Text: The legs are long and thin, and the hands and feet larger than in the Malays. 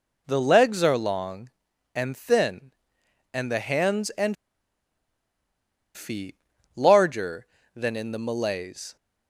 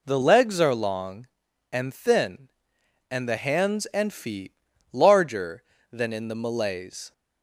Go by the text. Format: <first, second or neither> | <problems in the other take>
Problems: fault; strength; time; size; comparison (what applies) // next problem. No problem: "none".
second | pauses between "and" and "feet"; strong; at 4.3 s; 1.6 s long // pauses between "feet" and "larger"; at 6.3 s; 0.40 s long; also in the second